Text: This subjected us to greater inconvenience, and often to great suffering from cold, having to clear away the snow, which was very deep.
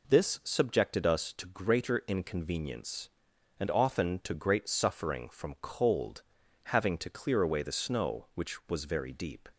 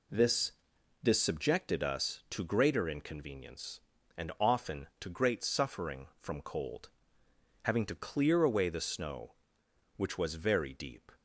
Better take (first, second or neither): first